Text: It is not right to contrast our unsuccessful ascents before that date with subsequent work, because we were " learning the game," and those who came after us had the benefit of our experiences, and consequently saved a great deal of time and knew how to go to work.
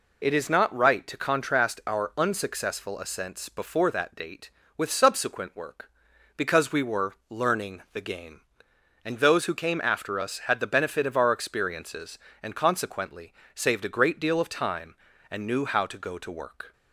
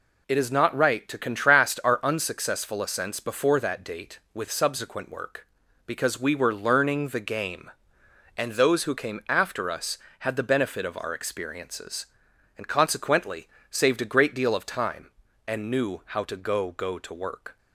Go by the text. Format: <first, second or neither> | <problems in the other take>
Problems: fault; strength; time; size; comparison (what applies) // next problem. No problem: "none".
first | pauses between "consequently" and "saved"; slight; at 13.4 s; 0.22 s long; slight in the first // says "go" twice; at 16.7 s